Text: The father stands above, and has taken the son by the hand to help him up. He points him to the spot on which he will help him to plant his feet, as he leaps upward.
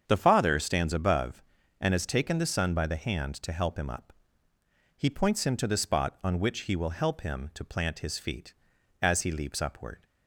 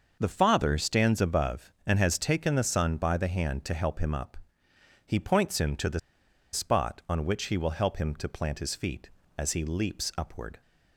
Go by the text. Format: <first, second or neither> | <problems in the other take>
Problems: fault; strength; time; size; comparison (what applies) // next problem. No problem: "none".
first | starts louder than the rest; until 1.2 s; 6 dB; strong in the first // pauses between "the" and "spot"; noticeable; at 5.9 s; 0.53 s long